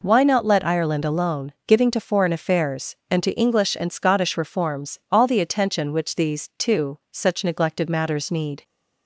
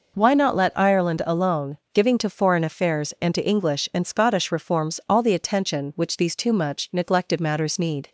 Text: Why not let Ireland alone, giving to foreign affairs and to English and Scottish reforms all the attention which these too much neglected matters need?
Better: second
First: says "such" for "much"; at 7.1 s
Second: none

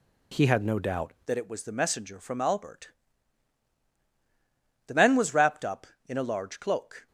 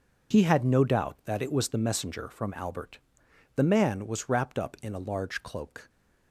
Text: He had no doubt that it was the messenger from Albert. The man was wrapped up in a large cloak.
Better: second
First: changes voice at "that"; from 1.2 s on; 5.8 s long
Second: none

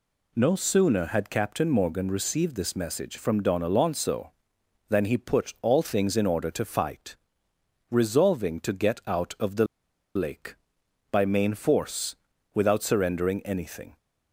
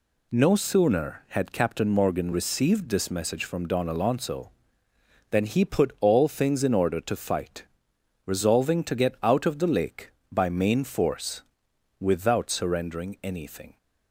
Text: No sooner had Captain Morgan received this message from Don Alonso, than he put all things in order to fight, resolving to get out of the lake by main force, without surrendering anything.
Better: second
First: pauses between "the" and "lake"; noticeable; at 9.6 s; 0.50 s long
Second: none

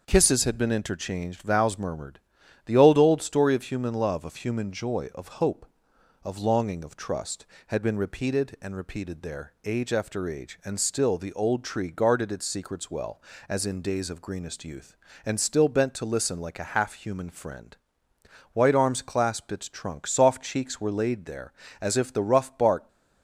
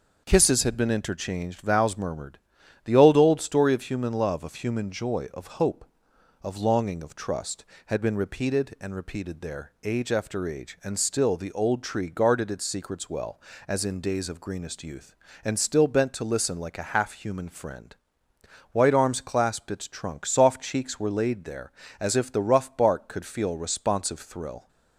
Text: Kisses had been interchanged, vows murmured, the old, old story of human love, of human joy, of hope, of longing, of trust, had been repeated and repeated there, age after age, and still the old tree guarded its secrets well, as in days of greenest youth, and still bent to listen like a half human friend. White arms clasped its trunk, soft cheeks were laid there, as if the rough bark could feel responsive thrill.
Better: second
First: starts louder than the rest; noticeable; until 1.0 s; 6 dB // stops before "could feel responsive thrill"; at 22.8 s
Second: starts louder than the rest; noticeable; until 1.2 s; 6 dB

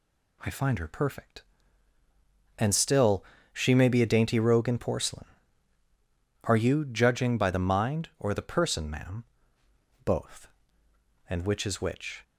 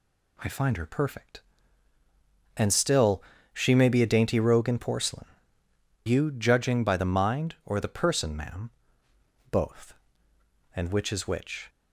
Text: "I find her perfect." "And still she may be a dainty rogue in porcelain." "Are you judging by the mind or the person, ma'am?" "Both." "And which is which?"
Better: first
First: pauses between "still" and "she"; slight; at 3.2 s; 0.30 s long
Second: pauses between "still" and "she"; slight; at 3.2 s; 0.32 s long // skips "Are"; at 5.6 s

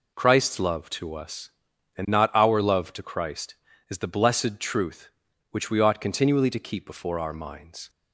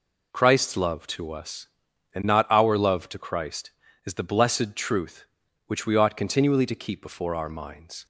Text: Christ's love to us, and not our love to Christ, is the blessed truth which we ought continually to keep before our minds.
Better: neither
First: none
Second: none

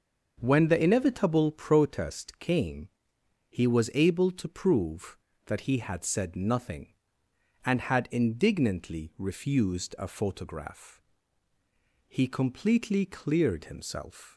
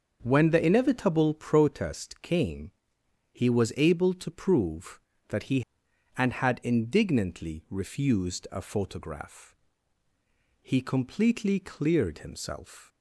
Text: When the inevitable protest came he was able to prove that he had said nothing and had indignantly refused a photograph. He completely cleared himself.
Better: first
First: pauses between "came" and "he"; noticeable; at 2.8 s; 0.60 s long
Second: starts louder than the rest; until 1.2 s; 6 dB // pauses between "came" and "he"; noticeable; at 2.7 s; 0.60 s long // skips "had said nothing"; at 5.8 s

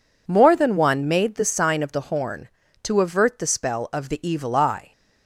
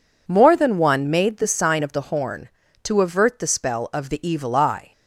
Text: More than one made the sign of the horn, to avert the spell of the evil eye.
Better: neither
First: none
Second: none

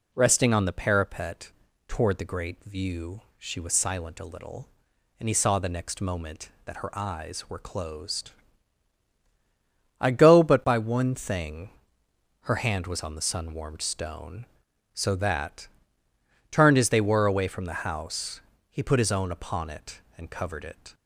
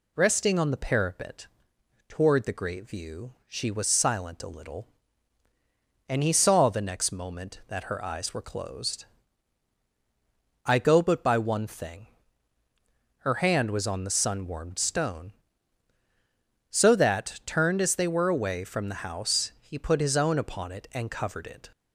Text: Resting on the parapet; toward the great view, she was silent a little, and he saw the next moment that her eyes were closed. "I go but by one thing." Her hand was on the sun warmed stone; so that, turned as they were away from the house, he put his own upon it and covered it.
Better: neither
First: none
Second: none

